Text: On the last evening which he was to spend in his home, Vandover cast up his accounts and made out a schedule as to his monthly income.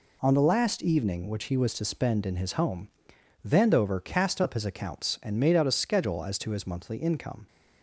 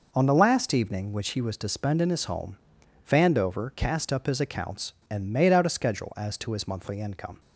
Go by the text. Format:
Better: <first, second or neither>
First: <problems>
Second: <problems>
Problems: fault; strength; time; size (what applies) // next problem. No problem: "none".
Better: neither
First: none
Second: none